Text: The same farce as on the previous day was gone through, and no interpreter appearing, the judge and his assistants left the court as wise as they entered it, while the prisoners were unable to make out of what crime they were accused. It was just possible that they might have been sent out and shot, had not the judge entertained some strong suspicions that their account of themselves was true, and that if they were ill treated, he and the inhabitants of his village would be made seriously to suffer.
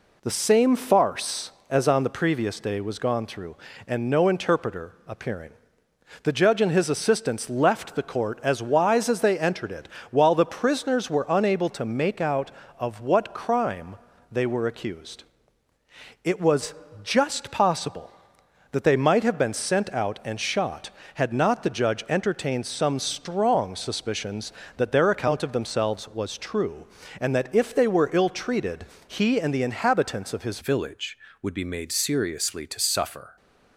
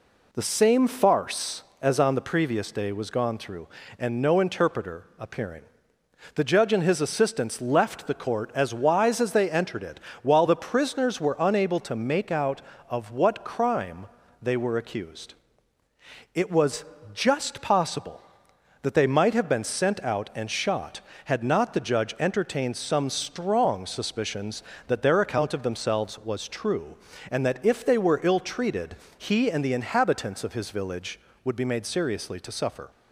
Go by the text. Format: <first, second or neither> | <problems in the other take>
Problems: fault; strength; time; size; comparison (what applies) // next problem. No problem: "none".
second | pauses between "crime" and "they"; slight; at 13.9 s; 0.36 s long; slight in the second // pauses between "was" and "just"; slight; at 16.7 s; 0.30 s long; slight in the second // changes voice at "village"; from 30.6 s on; 2.7 s long